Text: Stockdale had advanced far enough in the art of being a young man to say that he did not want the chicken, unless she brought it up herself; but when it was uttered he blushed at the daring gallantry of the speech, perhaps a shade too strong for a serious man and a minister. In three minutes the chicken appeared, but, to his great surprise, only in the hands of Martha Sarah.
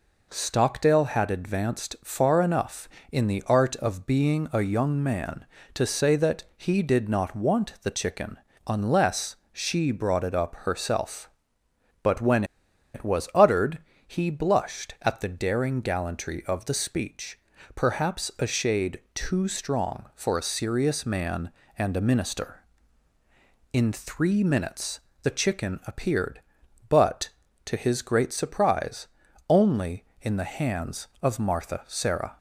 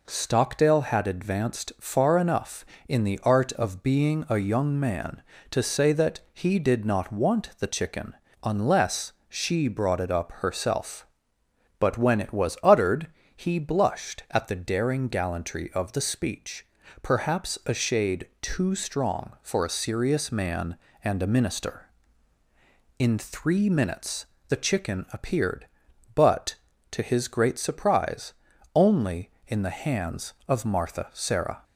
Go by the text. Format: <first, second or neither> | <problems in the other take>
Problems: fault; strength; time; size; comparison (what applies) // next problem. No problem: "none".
second | pauses between "unless" and "she"; slight; at 9.3 s; 0.16 s long; slight in the second // pauses between "when" and "it"; noticeable; at 12.4 s; 0.50 s long // pauses between "uttered" and "he"; slight; at 13.7 s; 0.28 s long; slight in the second // pauses between "shade" and "too"; slight; at 18.9 s; 0.16 s long; slight in the second // pauses between "minutes" and "the"; slight; at 24.9 s; 0.24 s long; slight in the second